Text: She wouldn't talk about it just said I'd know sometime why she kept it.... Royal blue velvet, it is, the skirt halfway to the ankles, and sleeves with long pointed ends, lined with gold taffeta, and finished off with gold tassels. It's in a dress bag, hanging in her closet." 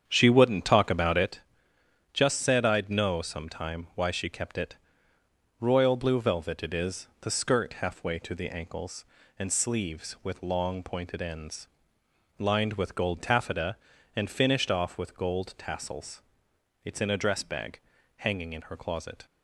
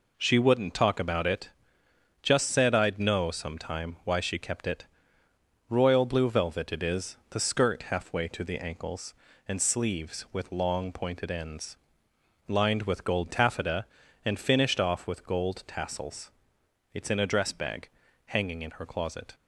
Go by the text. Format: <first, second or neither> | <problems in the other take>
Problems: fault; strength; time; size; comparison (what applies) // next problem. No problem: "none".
second | starts louder than the rest; strong; until 1.4 s; 8 dB // pauses between "it" and "just"; noticeable; at 1.4 s; 0.72 s long; noticeable in the second